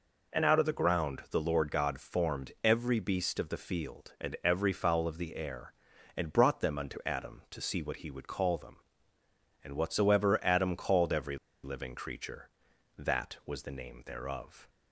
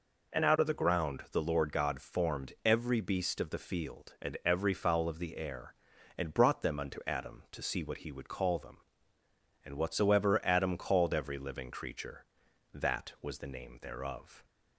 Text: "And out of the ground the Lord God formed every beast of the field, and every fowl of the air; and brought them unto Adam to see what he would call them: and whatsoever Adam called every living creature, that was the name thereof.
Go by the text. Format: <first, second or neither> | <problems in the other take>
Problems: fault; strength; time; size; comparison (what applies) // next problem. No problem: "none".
second | pauses between "every" and "living"; slight; at 11.3 s; 0.26 s long